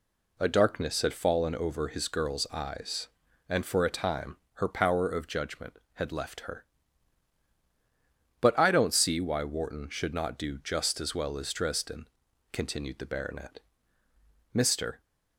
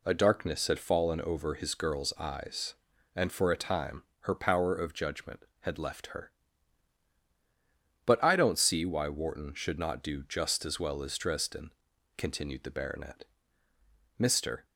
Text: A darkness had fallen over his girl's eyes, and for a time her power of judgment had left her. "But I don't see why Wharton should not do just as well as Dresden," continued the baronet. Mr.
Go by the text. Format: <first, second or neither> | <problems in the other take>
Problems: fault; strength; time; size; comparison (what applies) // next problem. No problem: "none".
neither | pauses between "time" and "her"; slight; the same in both